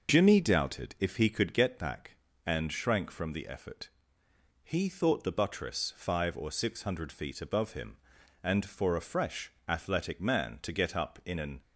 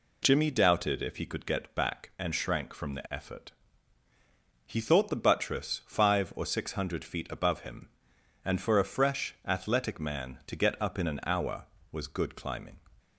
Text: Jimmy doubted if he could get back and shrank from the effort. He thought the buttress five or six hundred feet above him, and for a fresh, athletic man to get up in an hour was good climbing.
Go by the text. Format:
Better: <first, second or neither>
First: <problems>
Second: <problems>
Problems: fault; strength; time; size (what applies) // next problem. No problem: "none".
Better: second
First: stops before "hour was good climbing"; at 11.6 s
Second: none